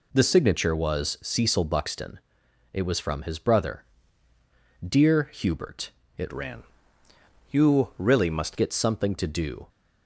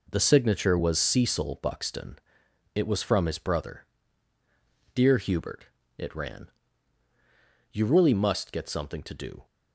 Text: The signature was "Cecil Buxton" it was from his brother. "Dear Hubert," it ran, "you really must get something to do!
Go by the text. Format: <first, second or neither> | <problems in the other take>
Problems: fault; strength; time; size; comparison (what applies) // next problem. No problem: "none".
second | pauses between "Buxton" and "it"; noticeable; at 2.1 s; 0.54 s long; noticeable in the second // changes voice from "ran" to "must"; from 6.3 to 8.5 s; 2.2 s long